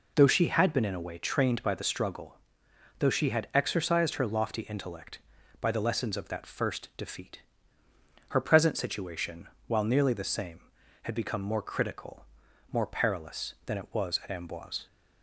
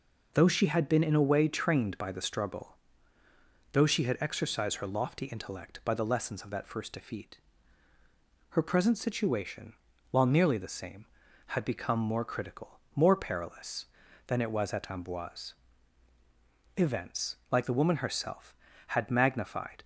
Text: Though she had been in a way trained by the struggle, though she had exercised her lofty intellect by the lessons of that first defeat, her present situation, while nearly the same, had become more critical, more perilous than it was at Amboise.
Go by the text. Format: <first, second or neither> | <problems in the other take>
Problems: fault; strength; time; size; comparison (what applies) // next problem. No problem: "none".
first | goes on to say "Events like the woman herself had magnified"; strong; from 16.7 s on; 3.0 s long